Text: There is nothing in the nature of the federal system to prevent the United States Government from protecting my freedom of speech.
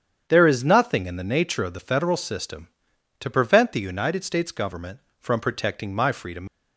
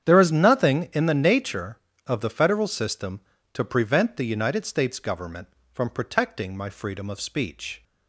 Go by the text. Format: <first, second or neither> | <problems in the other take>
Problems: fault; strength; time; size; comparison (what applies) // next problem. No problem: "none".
second | starts louder than the rest; strong; until 1.2 s; 8 dB; strong in the second // stops before "of speech"; at 6.4 s